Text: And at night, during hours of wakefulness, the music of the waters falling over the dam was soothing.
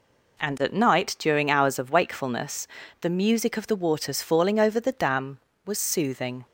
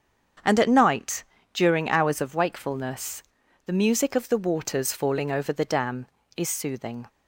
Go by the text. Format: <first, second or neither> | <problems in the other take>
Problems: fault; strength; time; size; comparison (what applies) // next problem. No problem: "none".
first | starts louder than the rest; strong; until 1.7 s; 7.5 dB // says "is" for "was"; at 6.3 s